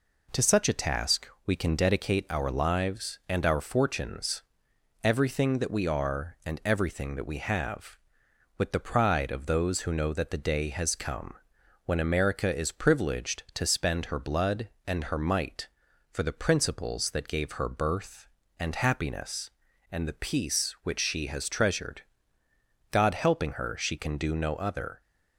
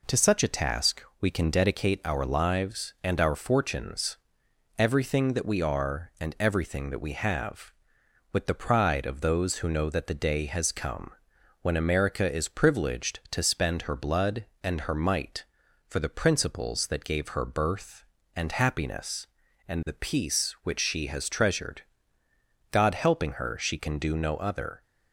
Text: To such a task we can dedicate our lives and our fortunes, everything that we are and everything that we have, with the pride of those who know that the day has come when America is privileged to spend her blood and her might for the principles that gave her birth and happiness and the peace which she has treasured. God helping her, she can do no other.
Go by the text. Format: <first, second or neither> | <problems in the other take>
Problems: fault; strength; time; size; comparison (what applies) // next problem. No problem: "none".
neither | pauses between "task" and "we"; slight; the same in both // pauses between "come" and "when"; noticeable; the same in both